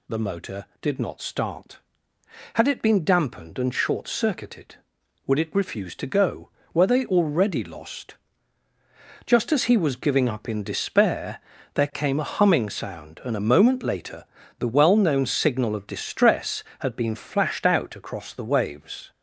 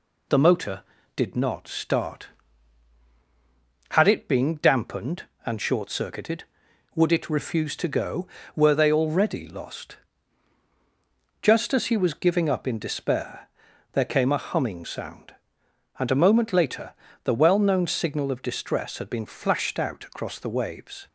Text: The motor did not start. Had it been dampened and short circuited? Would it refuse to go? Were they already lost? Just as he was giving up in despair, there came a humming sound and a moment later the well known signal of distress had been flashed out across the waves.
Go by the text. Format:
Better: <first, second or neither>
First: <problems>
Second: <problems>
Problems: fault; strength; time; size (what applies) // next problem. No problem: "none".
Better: neither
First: pauses between "later" and "the"; slight; at 14.2 s; 0.34 s long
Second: pauses between "later" and "the"; slight; at 16.9 s; 0.30 s long